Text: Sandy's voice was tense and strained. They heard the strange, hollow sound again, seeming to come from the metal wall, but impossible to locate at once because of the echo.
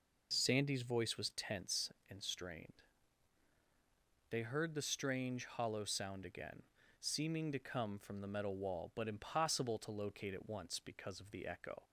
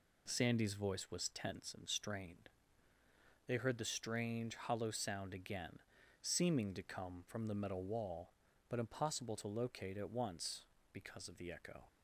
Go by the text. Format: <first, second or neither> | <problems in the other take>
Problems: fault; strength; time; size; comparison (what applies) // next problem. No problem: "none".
neither | none